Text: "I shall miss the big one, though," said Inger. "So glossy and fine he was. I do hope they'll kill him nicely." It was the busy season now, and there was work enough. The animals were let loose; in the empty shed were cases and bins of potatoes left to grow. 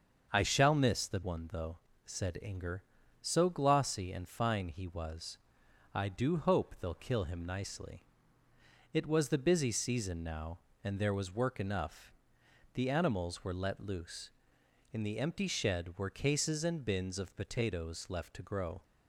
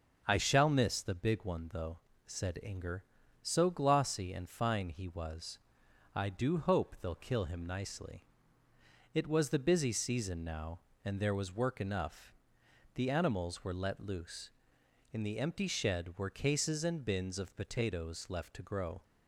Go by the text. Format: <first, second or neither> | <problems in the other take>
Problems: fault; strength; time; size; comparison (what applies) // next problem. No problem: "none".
second | starts louder than the rest; until 1.3 s; 7 dB; also in the second // skips "big"; at 1.2 s